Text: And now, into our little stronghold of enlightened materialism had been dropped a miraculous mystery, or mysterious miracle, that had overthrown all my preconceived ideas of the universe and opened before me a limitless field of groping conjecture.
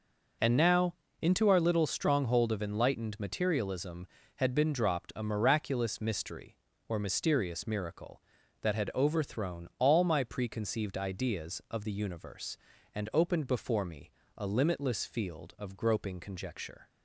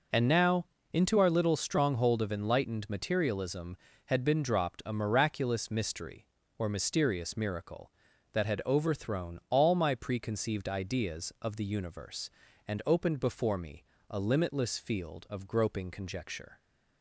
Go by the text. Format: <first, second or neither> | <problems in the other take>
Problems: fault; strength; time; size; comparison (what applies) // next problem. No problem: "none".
neither | pauses between "me" and "a"; slight; the same in both